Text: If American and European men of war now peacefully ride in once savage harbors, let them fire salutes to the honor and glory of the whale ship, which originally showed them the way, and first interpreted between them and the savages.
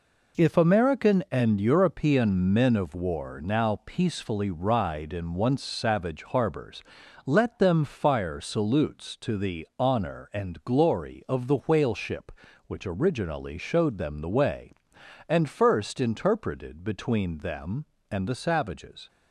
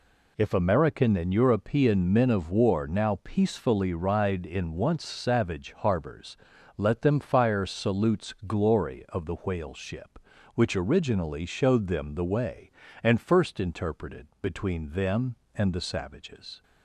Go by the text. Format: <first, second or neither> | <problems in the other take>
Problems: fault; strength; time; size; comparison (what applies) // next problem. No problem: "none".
first | skips "to the honor and"; at 8.3 s // pauses between "interpreted" and "between"; slight; at 14.2 s; 0.16 s long